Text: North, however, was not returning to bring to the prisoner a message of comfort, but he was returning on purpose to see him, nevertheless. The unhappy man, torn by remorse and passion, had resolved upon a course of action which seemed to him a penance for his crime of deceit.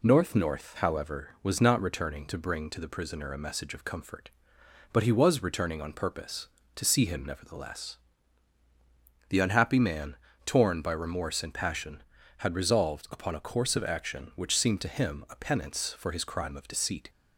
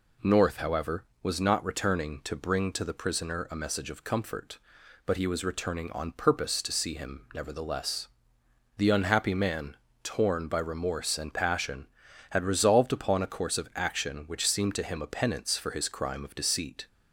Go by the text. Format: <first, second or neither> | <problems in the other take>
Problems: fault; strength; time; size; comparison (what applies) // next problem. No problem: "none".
second | says "North" twice; at 0.3 s